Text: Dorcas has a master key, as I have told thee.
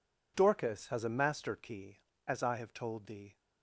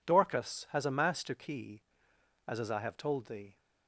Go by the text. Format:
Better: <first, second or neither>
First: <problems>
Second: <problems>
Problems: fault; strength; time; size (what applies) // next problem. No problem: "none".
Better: first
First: none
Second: says "as" twice; at 2.5 s